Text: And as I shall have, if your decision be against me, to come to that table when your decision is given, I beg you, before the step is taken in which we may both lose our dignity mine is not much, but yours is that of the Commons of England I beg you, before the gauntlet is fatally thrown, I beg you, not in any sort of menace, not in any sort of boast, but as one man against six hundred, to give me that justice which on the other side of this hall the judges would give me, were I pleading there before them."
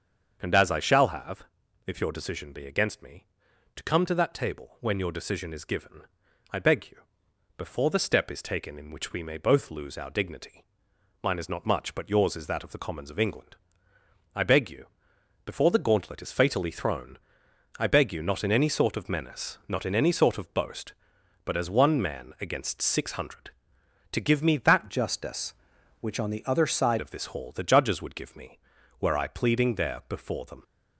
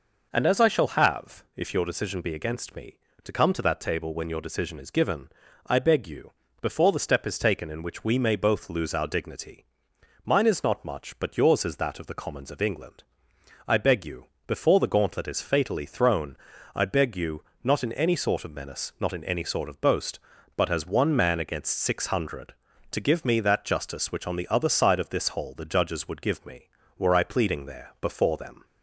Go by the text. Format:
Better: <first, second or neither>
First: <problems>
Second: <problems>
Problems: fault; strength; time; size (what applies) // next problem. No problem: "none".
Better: second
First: starts louder than the rest; until 1.4 s; 7 dB // pauses between "dignity" and "mine"; noticeable; at 10.6 s; 0.60 s long // pauses between "England" and "I"; noticeable; at 13.5 s; 0.80 s long // changes voice from "justice" to "side"; from 24.9 to 27.0 s; 2.1 s long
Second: pauses between "dignity" and "mine"; noticeable; at 9.6 s; 0.60 s long // pauses between "England" and "I"; noticeable; at 13.0 s; 0.64 s long